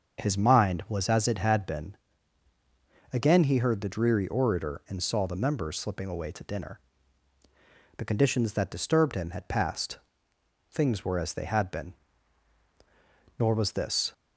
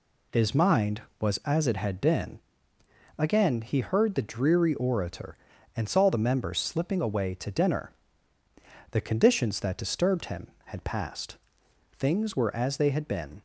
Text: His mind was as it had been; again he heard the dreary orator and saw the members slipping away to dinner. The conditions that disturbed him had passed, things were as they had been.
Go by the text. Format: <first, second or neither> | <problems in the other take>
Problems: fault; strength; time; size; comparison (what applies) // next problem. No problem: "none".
second | starts louder than the rest; until 1.2 s; 6.5 dB // goes on to say "Nor was this"; noticeable; from 13.3 s on; 0.74 s long